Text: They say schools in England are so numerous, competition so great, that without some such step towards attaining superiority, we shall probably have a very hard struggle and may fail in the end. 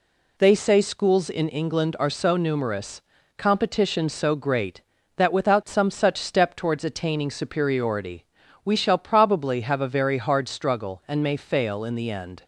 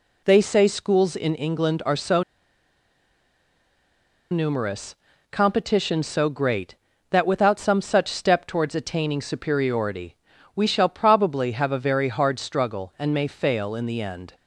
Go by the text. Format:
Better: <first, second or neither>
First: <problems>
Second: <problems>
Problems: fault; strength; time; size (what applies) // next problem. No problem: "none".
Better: first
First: none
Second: pauses between "so" and "numerous"; strong; at 2.2 s; 2.1 s long